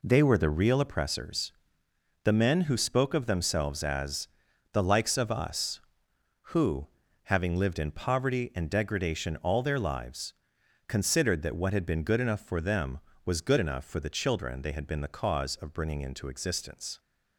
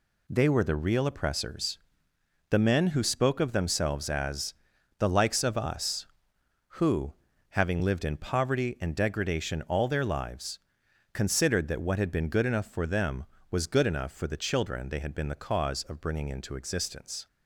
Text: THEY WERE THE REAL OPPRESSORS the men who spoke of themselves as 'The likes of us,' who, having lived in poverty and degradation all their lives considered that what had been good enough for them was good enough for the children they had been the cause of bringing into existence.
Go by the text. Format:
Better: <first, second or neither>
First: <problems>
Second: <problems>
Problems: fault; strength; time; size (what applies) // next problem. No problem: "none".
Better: second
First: starts louder than the rest; slight; until 1.0 s; 3 dB // pauses between "OPPRESSORS" and "the"; noticeable; at 1.5 s; 0.70 s long // pauses between "as" and "The"; noticeable; at 4.2 s; 0.46 s long // pauses between "lives" and "considered"; noticeable; at 10.3 s; 0.54 s long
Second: pauses between "OPPRESSORS" and "the"; noticeable; at 1.7 s; 0.70 s long // pauses between "as" and "The"; noticeable; at 4.5 s; 0.46 s long // pauses between "lives" and "considered"; noticeable; at 10.5 s; 0.54 s long